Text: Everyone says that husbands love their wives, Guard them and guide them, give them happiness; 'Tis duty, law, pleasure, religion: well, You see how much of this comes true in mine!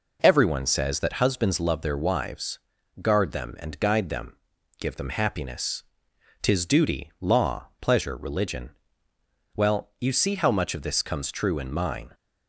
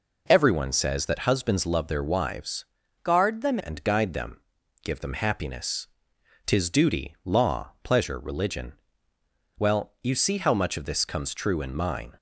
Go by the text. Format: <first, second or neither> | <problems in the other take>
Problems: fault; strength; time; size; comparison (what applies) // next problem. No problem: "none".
first | changes voice from "Guard" to "them"; from 3.0 to 3.5 s; 0.5 s long